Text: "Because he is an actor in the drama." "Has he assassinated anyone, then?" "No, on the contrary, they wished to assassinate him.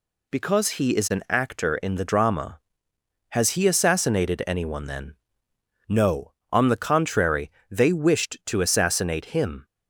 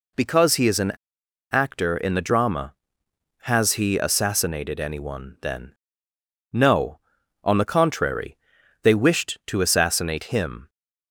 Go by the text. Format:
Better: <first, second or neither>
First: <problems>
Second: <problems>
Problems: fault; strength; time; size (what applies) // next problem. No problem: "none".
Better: first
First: none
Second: pauses between "an" and "actor"; noticeable; at 0.9 s; 0.59 s long